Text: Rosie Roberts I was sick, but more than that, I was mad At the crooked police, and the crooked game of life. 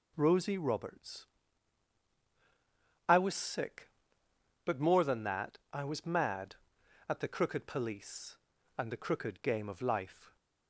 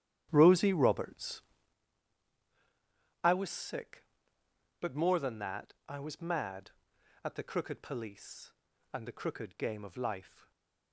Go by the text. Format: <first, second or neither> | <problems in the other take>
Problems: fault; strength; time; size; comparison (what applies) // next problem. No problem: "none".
first | starts louder than the rest; strong; until 1.8 s; 10.5 dB // pauses between "Roberts" and "I"; strong; at 1.4 s; 1.8 s long; strong in the first // stays silent after the last word; slight; from 10.2 s on; 0.7 s long